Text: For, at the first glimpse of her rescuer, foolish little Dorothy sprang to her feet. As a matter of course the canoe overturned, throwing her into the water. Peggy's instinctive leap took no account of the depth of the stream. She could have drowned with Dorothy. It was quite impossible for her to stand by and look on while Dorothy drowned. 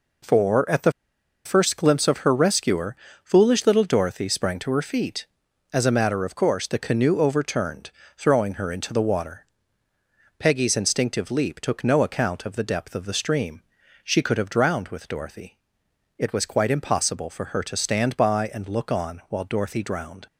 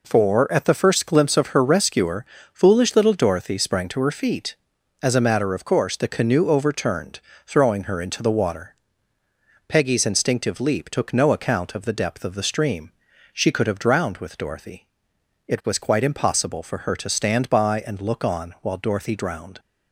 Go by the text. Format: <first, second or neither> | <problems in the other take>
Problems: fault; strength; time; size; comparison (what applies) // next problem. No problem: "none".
second | pauses between "the" and "first"; noticeable; at 0.9 s; 0.53 s long